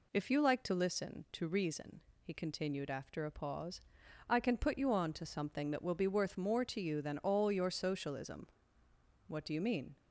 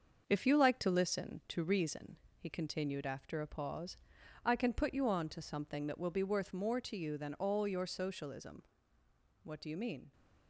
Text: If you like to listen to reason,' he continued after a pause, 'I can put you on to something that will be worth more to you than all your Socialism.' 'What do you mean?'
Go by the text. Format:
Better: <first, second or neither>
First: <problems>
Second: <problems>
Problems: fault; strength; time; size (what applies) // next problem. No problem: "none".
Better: first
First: none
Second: gets quieter; noticeable; throughout; 5 dB